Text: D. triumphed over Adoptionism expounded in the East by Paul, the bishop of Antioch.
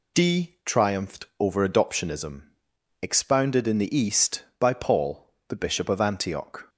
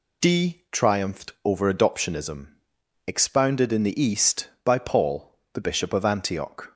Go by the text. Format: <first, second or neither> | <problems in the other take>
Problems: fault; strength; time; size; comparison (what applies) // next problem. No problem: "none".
neither | pauses between "Adoptionism" and "expounded"; noticeable; the same in both